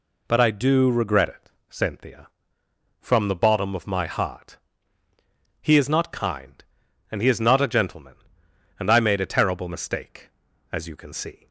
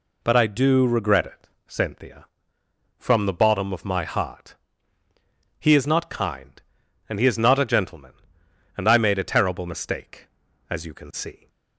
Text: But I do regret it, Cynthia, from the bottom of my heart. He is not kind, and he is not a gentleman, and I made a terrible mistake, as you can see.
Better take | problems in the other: neither | none

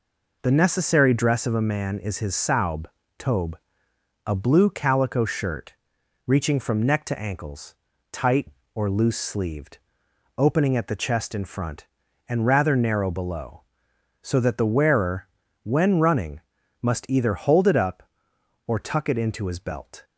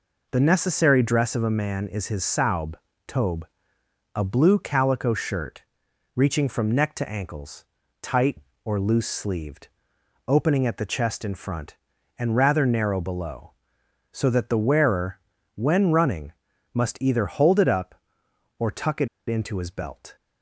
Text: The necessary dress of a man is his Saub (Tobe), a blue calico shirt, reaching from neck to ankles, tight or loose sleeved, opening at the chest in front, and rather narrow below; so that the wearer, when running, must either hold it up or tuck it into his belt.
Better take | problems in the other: first | pauses between "it" and "into"; slight; at 19.0 s; 0.19 s long

